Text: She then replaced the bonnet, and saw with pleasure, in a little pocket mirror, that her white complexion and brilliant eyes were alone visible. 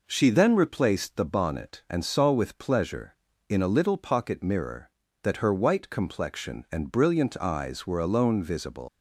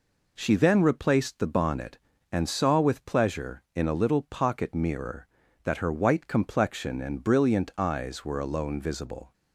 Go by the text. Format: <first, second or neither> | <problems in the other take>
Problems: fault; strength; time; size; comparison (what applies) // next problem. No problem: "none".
second | leaves "visible" unfinished; at 8.8 s; 130 ms